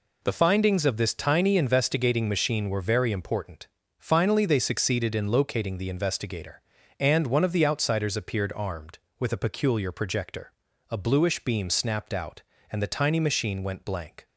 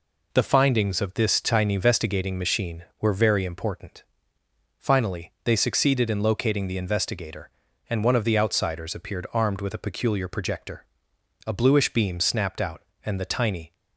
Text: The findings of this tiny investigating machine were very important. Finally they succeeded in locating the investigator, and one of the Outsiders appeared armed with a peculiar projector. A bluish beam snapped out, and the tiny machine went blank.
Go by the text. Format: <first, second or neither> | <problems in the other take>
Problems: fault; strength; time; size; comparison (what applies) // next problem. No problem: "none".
first | stops before "machine went blank"; at 13.7 s